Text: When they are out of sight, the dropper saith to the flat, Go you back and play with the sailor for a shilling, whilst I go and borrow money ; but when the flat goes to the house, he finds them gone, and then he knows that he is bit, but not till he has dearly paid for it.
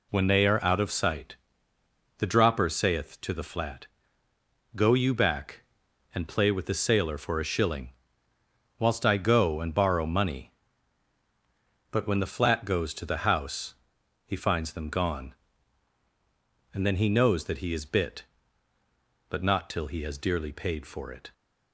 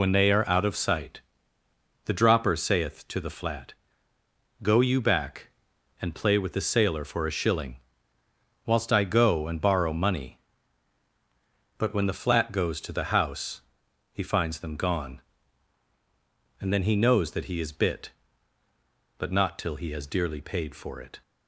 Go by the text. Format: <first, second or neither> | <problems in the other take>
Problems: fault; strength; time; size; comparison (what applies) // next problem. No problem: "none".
first | loses the start of "When"; at 0.0 s; 45 ms